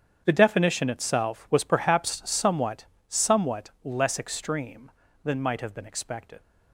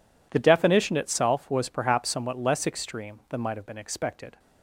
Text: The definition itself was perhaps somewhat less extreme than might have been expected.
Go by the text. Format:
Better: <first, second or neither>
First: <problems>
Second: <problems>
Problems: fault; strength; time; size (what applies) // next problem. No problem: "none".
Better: second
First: starts louder than the rest; strong; until 1.2 s; 8.5 dB // says "somewhat" twice; at 3.0 s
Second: none